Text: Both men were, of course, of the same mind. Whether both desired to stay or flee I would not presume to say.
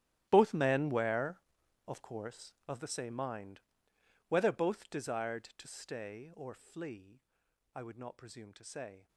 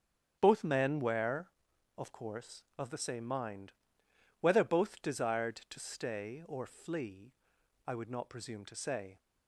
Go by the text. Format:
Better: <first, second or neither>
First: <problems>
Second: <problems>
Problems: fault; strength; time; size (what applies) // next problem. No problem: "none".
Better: second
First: gets quieter; strong; throughout; 18 dB // starts louder than the rest; strong; until 1.3 s; 13 dB // pauses between "flee" and "I"; noticeable; at 7.1 s; 0.56 s long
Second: starts louder than the rest; strong; until 1.4 s; 8 dB // pauses between "flee" and "I"; noticeable; at 7.3 s; 0.56 s long